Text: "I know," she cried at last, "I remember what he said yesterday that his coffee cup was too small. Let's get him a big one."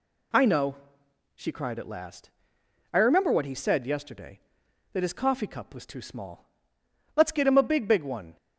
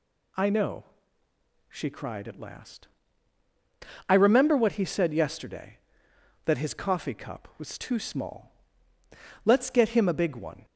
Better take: second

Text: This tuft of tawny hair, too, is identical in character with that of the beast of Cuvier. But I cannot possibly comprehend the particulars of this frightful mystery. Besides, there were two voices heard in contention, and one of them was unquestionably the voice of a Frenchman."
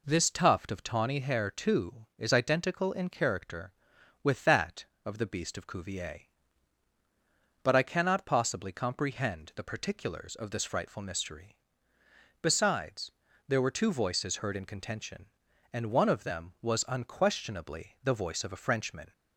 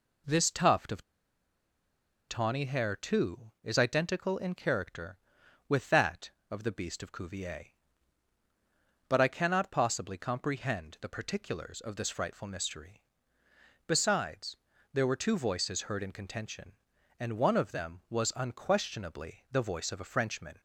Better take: first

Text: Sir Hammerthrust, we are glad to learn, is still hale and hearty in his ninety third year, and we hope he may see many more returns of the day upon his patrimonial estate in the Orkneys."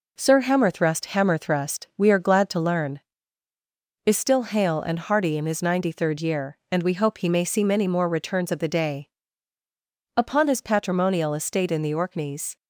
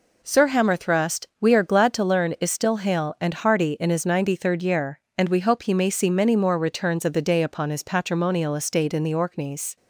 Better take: second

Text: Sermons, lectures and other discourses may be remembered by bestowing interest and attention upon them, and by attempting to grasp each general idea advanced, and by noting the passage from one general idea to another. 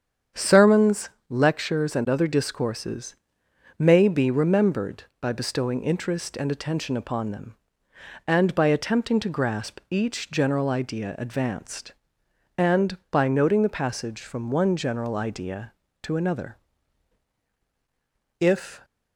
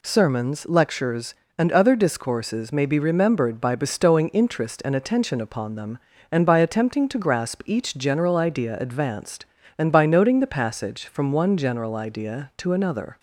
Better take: second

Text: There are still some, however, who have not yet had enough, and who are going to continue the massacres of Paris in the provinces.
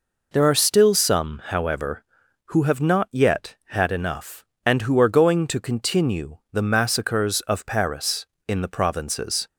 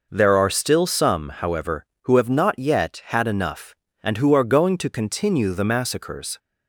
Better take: first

